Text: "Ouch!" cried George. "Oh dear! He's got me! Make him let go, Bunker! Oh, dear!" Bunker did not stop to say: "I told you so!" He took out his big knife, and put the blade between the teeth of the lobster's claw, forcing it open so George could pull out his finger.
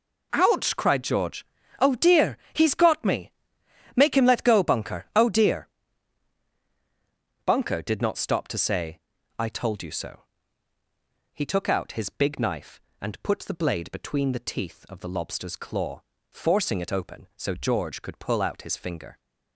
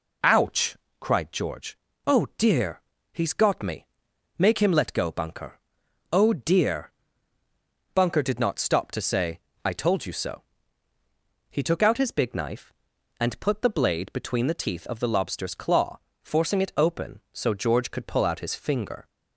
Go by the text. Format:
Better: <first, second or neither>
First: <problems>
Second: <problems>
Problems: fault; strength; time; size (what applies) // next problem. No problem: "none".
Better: neither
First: none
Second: none